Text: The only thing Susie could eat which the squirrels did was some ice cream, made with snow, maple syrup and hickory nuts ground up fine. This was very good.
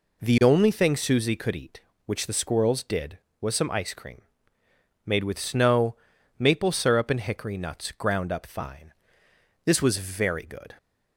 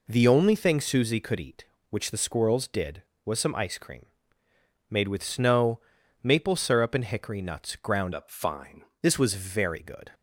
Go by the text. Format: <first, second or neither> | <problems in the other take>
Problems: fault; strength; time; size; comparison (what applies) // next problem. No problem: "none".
first | changes voice from "up" to "fine"; from 8.1 to 8.8 s; 0.7 s long